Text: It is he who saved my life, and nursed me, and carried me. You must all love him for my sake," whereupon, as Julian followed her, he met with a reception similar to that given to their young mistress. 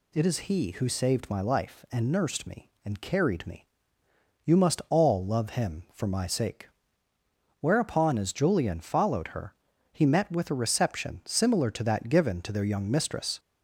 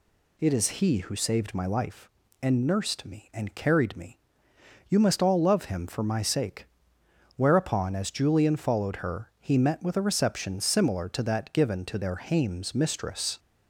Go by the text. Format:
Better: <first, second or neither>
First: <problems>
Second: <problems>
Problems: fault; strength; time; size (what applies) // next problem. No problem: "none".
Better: first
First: none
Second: says "hames" for "young"; at 12.1 s